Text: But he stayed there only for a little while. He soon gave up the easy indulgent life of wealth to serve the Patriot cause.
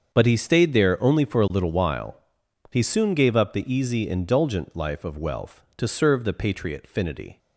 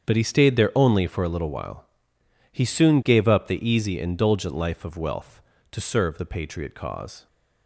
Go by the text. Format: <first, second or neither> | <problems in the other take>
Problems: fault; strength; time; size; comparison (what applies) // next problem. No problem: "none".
second | starts louder than the rest; until 1.1 s; 7 dB; strong in the second // says "finity" for "cause"; at 6.9 s